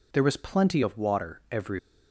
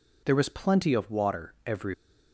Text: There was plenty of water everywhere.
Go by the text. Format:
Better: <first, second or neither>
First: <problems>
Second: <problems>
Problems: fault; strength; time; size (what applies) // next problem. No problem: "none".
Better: neither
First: none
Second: none